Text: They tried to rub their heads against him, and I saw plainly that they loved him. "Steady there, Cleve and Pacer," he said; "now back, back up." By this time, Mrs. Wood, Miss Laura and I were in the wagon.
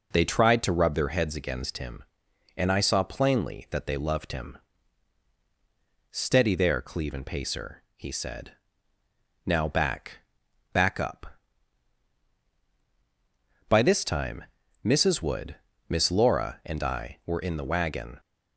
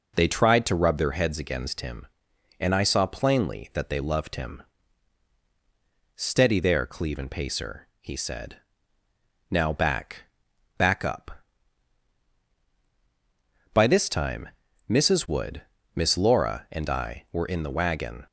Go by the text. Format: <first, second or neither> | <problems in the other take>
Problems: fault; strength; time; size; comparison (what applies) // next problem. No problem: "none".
neither | none